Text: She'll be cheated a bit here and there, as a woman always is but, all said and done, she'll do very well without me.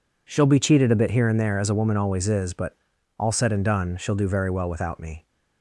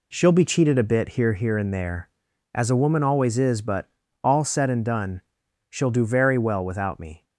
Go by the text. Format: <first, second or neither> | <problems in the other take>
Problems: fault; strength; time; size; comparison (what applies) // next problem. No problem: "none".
first | says "here" twice; at 1.3 s